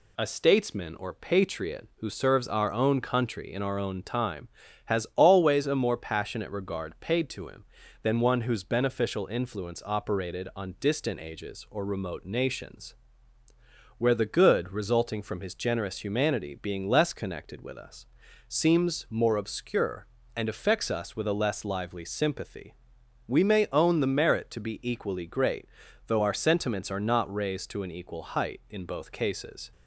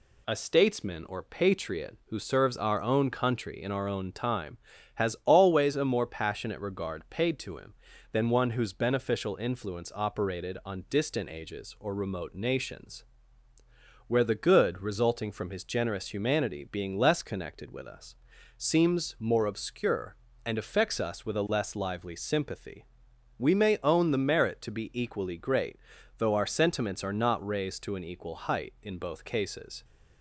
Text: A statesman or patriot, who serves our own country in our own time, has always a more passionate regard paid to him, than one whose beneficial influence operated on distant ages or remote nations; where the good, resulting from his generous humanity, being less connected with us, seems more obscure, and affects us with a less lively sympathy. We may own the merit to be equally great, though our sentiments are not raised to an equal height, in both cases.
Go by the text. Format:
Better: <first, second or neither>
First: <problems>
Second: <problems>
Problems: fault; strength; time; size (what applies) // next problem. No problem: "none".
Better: neither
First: none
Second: none